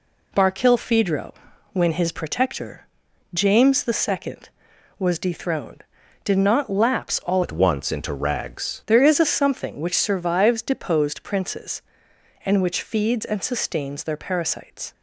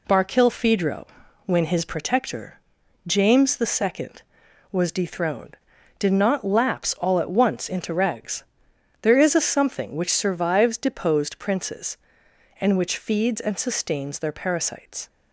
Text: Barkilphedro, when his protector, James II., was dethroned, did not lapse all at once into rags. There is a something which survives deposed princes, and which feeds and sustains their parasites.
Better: second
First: changes voice from "at" to "rags"; from 7.4 to 8.8 s; 1.4 s long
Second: none

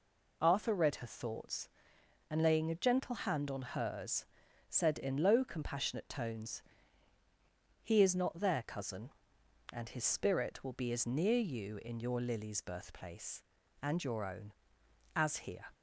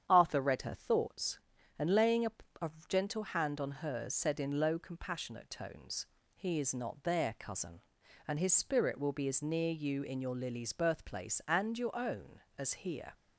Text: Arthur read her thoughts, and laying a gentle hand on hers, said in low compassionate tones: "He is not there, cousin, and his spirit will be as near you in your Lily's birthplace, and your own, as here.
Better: first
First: none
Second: starts louder than the rest; strong; until 1.0 s; 9 dB // says "a" twice; at 2.6 s

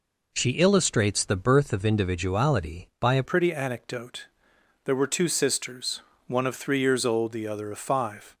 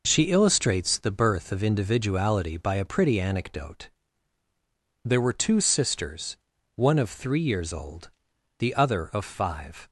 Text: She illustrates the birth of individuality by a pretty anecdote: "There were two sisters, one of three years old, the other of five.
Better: second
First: changes voice at "pretty"; from 3.2 s on; 5.1 s long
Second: none

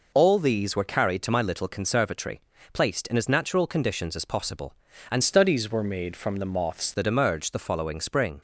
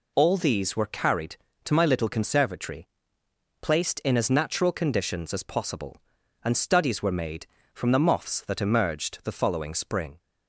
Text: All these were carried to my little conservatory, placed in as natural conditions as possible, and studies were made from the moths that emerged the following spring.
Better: second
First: changes voice from "studies" to "moths"; from 5.2 to 6.9 s; 1.7 s long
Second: none

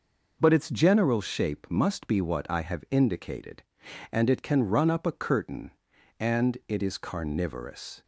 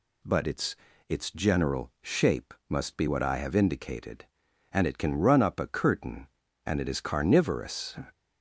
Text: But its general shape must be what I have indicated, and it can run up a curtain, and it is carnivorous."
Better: first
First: none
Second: says "its" twice; at 1.0 s

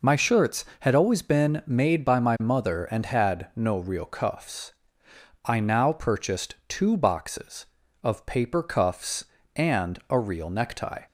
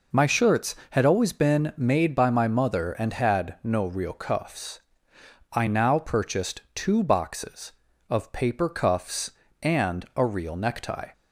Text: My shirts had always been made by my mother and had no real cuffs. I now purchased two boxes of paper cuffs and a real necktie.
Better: neither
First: none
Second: none

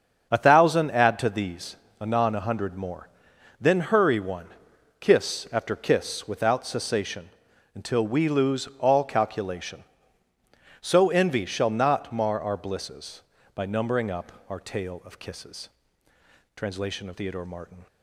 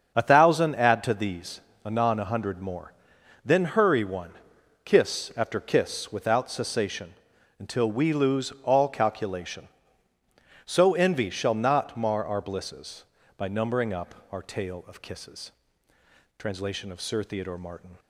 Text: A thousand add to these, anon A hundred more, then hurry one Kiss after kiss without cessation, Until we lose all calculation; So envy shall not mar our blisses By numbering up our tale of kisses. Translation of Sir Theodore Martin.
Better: second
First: starts louder than the rest; until 1.3 s; 7 dB // pauses between "one" and "Kiss"; noticeable; at 4.4 s; 0.50 s long // pauses between "up" and "our"; slight; at 14.3 s; 0.16 s long // skips "Sir"; at 17.1 s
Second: starts louder than the rest; until 1.1 s; 7 dB // pauses between "one" and "Kiss"; noticeable; at 4.3 s; 0.50 s long // pauses between "up" and "our"; slight; at 14.1 s; 0.16 s long

